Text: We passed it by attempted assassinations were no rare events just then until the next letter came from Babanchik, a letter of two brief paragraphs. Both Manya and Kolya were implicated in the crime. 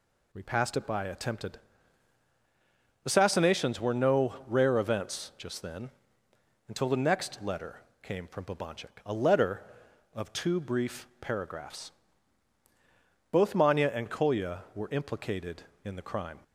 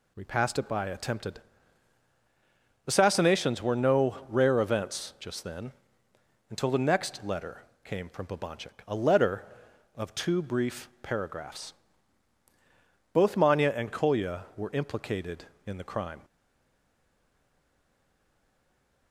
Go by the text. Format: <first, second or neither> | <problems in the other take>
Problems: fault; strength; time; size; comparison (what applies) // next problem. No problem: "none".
first | pauses between "attempted" and "assassinations"; strong; at 1.3 s; 1.4 s long; strong in the first // pauses between "then" and "until"; noticeable; at 5.7 s; 0.78 s long; noticeable in the first // pauses between "letter" and "came"; slight; at 7.6 s; 0.20 s long; slight in the first // stays silent after the last word; strong; from 16.2 s on; 2.9 s long